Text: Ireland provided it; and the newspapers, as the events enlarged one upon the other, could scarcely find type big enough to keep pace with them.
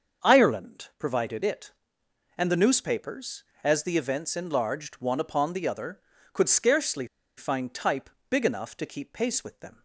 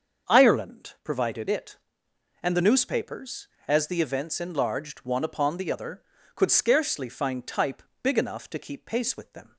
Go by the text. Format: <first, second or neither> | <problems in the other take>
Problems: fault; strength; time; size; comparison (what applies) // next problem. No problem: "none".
second | starts louder than the rest; until 1.3 s; 6.5 dB; also in the second // pauses between "scarcely" and "find"; slight; at 7.0 s; 0.31 s long // pauses between "type" and "big"; slight; at 8.0 s; 0.20 s long; slight in the second